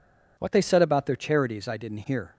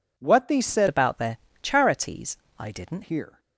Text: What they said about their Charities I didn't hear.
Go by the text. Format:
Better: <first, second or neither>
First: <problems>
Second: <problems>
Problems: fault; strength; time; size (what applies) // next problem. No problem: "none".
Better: first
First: none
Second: changes voice from "about" to "didn't"; from 0.8 to 3.0 s; 2.2 s long // pauses between "their" and "Charities"; slight; at 1.3 s; 0.26 s long // pauses between "Charities" and "I"; slight; at 2.3 s; 0.22 s long